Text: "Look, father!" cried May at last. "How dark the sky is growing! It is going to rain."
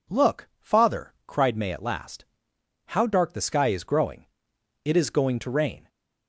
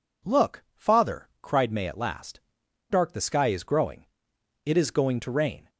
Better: first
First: none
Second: skips "How"; at 2.6 s

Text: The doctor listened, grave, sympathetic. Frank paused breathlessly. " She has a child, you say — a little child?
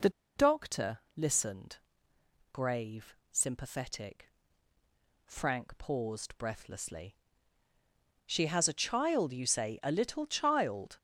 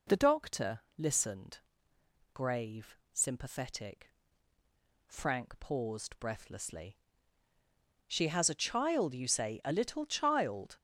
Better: second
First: pauses between "The" and "doctor"; slight; at 0.0 s; 0.26 s long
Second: none

